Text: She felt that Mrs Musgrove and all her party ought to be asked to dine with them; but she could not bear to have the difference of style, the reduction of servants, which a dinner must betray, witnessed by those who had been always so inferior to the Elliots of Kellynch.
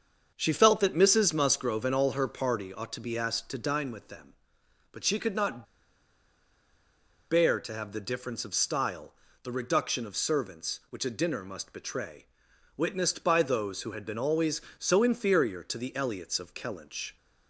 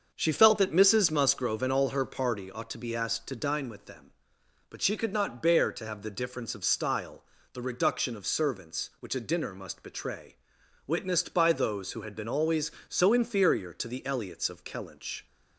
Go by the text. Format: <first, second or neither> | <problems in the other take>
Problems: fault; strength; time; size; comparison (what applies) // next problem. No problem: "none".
second | starts louder than the rest; until 1.3 s; 7 dB; also in the second // pauses between "not" and "bear"; strong; at 5.6 s; 1.6 s long